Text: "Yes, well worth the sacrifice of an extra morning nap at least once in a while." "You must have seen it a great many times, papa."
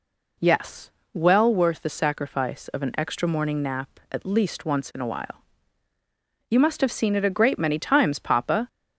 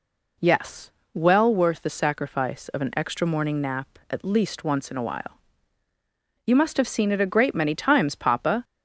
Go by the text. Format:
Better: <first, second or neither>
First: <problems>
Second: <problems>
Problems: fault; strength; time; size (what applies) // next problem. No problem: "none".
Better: neither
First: none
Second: none